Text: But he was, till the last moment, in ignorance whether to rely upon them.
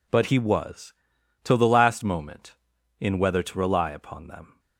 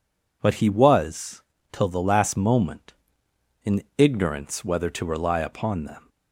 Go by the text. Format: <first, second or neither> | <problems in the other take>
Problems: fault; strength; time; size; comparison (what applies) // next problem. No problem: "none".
second | skips "ignorance"; at 3.1 s